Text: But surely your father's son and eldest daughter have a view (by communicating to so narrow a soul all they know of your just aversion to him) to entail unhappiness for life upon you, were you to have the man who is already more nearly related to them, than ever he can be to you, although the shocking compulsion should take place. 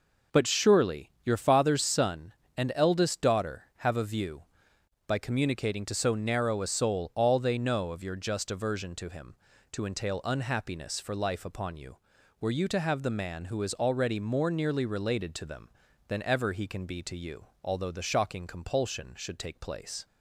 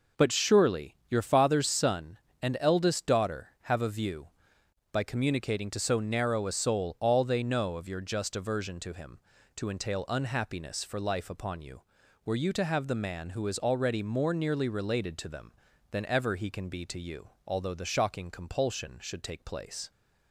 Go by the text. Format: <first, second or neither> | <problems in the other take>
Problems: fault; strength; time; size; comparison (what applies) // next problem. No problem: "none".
neither | none